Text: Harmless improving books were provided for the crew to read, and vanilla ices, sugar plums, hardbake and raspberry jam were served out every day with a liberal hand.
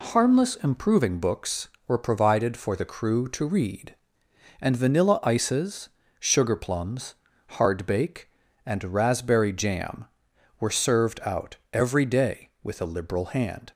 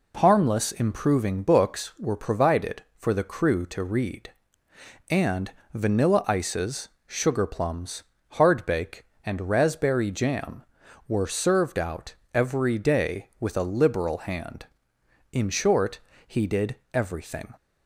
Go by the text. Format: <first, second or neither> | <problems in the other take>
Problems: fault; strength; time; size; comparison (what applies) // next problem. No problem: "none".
first | pauses between "and" and "vanilla"; slight; at 5.5 s; 0.22 s long // pauses between "out" and "every"; slight; at 12.1 s; 0.20 s long; slight in the first // goes on to say "In short he did everything"; strong; from 15.3 s on; 2.2 s long